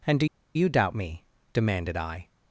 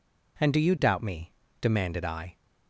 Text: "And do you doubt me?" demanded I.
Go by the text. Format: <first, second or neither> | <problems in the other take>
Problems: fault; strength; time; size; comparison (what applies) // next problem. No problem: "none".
second | pauses between "do" and "you"; slight; at 0.2 s; 0.29 s long